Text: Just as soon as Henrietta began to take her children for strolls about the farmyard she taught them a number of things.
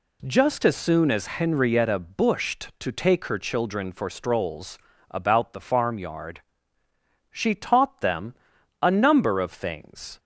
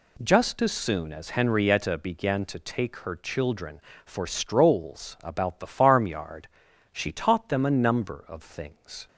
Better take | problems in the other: second | says "bushed" for "began"; at 1.9 s // pauses between "strolls" and "about"; slight; at 4.7 s; 0.32 s long // pauses between "farmyard" and "she"; noticeable; at 6.4 s; 0.90 s long; also in the second // pauses between "them" and "a"; noticeable; at 8.3 s; 0.48 s long

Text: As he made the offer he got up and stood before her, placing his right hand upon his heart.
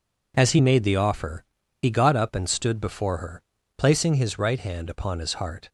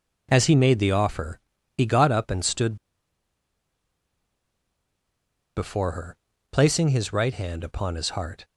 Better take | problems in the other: first | pauses between "offer" and "he"; slight; at 1.3 s; 0.36 s long; slight in the first // pauses between "stood" and "before"; strong; at 2.7 s; 2.8 s long

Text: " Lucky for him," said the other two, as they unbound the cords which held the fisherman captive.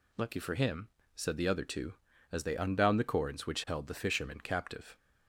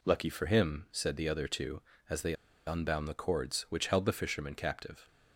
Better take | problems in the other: first | pauses between "they" and "unbound"; slight; at 2.3 s; 0.33 s long

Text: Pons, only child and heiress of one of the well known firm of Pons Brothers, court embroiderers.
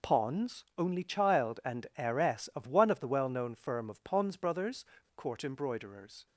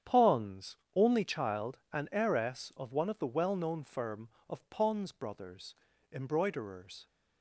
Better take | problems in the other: first | starts louder than the rest; strong; until 1.2 s; 9 dB // skips "court"; at 5.9 s

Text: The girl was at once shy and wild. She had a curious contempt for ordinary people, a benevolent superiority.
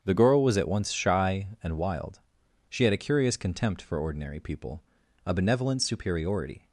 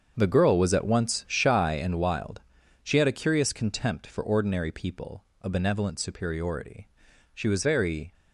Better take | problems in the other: first | starts louder than the rest; until 1.1 s; 7 dB; strong in the first // goes on to say "She was very"; noticeable; from 7.3 s on; 0.80 s long

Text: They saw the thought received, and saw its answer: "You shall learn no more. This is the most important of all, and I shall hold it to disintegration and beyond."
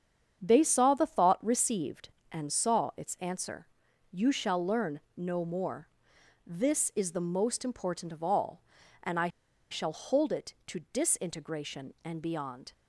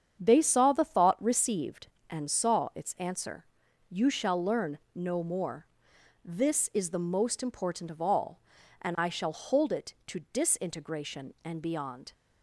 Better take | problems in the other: second | starts louder than the rest; strong; until 1.4 s; 8 dB; strong in the second // pauses between "I" and "shall"; at 9.2 s; 0.42 s long

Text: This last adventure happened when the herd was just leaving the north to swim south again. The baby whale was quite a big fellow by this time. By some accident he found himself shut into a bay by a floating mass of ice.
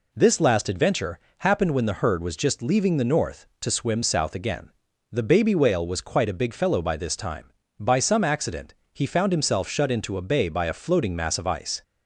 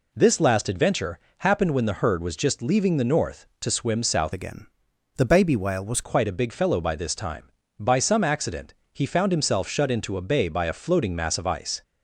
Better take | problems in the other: first | pauses between "adventure" and "happened"; slight; at 1.1 s; 0.20 s long; slight in the first // changes voice from "again" to "was"; from 4.3 to 6.0 s; 1.7 s long // pauses between "accident" and "he"; slight; at 8.7 s; 0.18 s long; slight in the first

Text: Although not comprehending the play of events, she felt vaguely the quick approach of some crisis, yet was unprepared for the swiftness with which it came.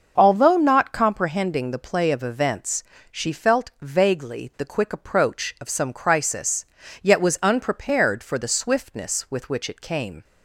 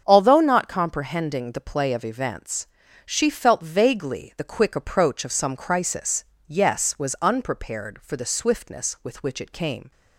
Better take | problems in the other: first | starts louder than the rest; until 1.0 s; 7 dB; noticeable in the first // says "yes" for "yet"; at 6.4 s

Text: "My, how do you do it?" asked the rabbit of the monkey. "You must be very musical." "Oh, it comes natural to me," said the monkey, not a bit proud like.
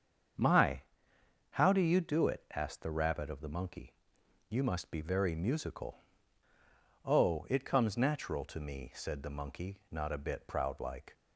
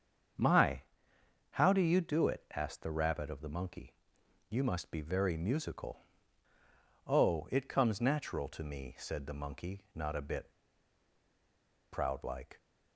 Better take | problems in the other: first | starts louder than the rest; strong; until 2.0 s; 7.5 dB; strong in the first // pauses between "bit" and "proud"; strong; at 10.5 s; 1.4 s long

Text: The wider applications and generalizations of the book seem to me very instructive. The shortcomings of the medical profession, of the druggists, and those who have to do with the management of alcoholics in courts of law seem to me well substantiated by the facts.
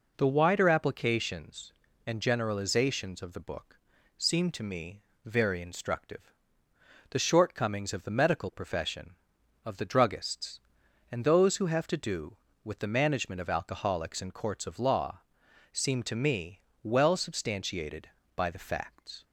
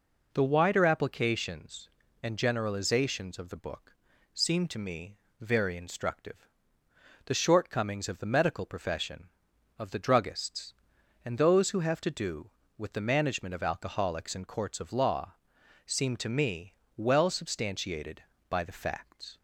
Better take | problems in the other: neither | pauses between "book" and "seem"; slight; the same in both // pauses between "me" and "very"; slight; the same in both // pauses between "law" and "seem"; noticeable; the same in both // pauses between "me" and "well"; slight; the same in both

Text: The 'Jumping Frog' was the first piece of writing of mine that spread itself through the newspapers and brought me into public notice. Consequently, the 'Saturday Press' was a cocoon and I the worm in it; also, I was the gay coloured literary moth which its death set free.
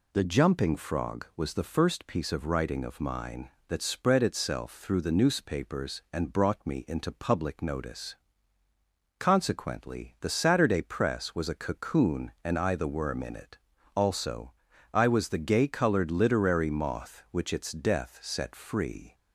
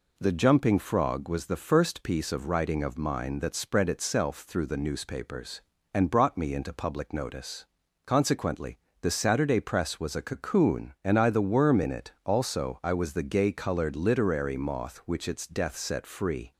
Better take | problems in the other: neither | none

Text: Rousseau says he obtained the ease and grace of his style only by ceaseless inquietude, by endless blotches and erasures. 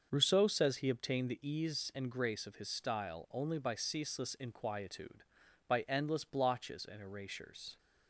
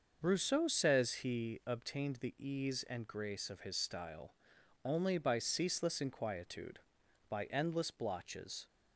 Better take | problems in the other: first | starts louder than the rest; noticeable; until 1.3 s; 6 dB; also in the first // pauses between "style" and "only"; noticeable; at 4.3 s; 0.50 s long // stops before "and erasures"; at 8.6 s

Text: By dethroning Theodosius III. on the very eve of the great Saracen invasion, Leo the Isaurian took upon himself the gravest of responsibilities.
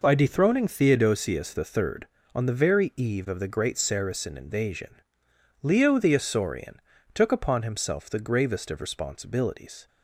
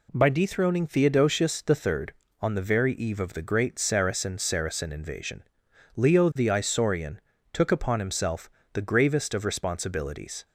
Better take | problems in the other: first | says "Saracen" twice; at 4.3 s // pauses between "Isaurian" and "took"; slight; at 7.1 s; 0.32 s long; slight in the first // pauses between "himself" and "the"; slight; at 8.5 s; 0.24 s long

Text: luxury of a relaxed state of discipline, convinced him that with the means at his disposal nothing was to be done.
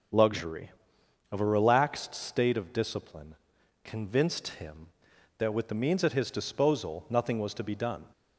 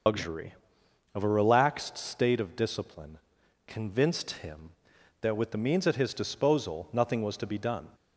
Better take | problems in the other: first | loses the start of "luxury"; at 0.0 s; 115 ms // starts louder than the rest; noticeable; until 1.6 s; 6 dB

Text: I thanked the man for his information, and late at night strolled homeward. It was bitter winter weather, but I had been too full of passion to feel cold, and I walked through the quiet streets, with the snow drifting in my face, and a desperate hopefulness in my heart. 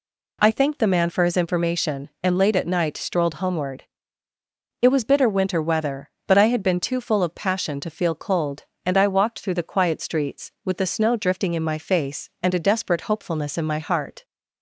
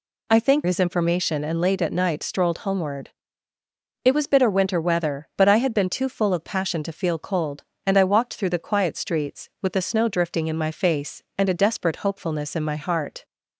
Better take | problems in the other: first | skips "the man for"; at 0.6 s

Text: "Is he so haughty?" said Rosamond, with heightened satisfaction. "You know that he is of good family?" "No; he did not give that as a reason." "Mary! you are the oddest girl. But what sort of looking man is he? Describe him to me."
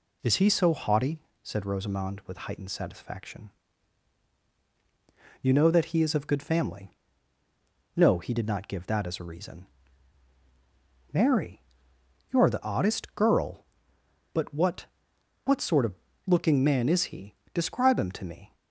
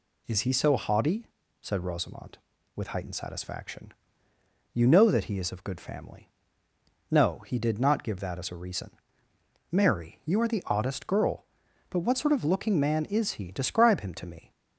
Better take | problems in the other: second | says "what" twice; at 15.4 s // pauses between "of" and "looking"; slight; at 15.9 s; 0.32 s long

